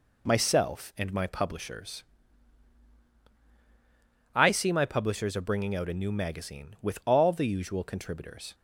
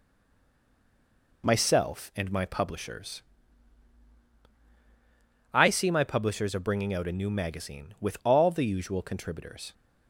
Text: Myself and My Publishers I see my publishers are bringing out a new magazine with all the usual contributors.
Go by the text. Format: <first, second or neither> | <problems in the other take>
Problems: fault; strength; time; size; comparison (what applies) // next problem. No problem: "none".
first | stays silent before the first word; noticeable; until 1.4 s; 1.4 s long // pauses between "Publishers" and "I"; strong; at 3.2 s; 2.3 s long; strong in the first